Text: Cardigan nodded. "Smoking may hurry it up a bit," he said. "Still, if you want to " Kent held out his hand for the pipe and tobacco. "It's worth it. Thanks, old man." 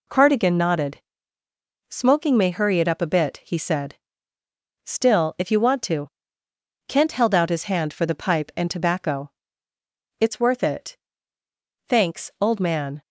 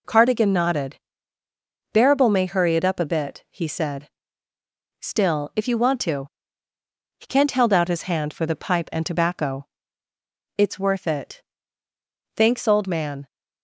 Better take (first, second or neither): first